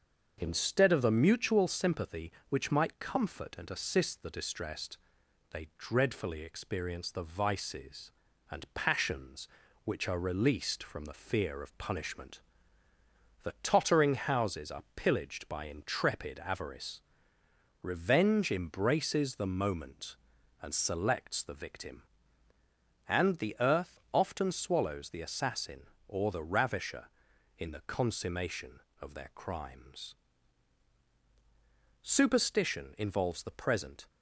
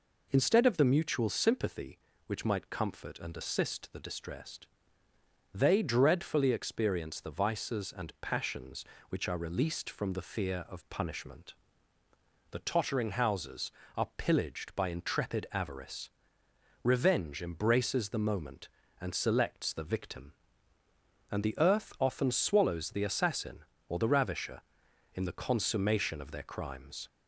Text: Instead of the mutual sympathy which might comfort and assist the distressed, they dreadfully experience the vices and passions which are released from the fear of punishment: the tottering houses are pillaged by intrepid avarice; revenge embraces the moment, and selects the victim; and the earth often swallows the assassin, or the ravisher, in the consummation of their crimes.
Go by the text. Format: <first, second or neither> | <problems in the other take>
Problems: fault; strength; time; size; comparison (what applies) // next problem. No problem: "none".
second | starts louder than the rest; until 1.3 s; 6.5 dB // goes on to say "Superstition involves the present"; strong; from 32.0 s on; 2.0 s long